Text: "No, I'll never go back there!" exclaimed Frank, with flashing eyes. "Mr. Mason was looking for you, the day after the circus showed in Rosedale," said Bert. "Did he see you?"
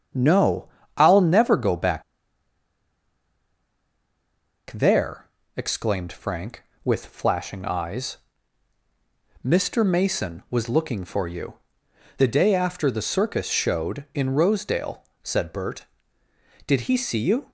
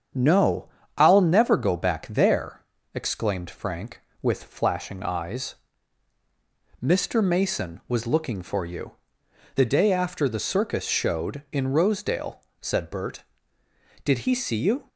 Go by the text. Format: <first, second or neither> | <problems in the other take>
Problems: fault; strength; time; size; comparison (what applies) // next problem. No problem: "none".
second | starts louder than the rest; strong; until 1.4 s; 8 dB; strong in the second // pauses between "back" and "there"; strong; at 2.0 s; 2.6 s long